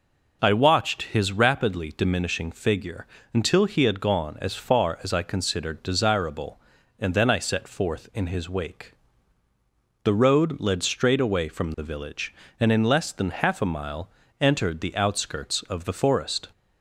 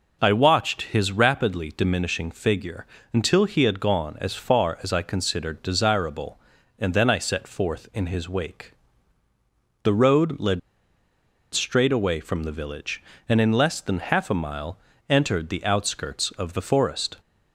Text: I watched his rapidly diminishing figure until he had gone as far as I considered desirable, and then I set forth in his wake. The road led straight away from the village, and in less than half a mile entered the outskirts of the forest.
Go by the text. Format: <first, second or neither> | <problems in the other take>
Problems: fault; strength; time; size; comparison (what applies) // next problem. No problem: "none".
first | pauses between "figure" and "until"; slight; at 2.8 s; 0.28 s long; slight in the first // pauses between "led" and "straight"; noticeable; at 10.5 s; 0.93 s long // pauses between "mile" and "entered"; slight; at 14.7 s; 0.32 s long; slight in the first